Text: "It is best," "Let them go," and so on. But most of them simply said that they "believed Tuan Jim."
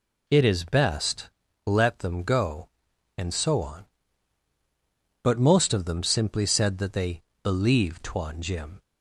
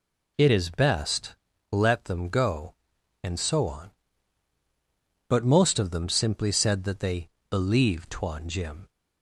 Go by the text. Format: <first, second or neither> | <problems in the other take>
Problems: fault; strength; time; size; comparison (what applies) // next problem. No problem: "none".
neither | pauses between "they" and "believed"; slight; the same in both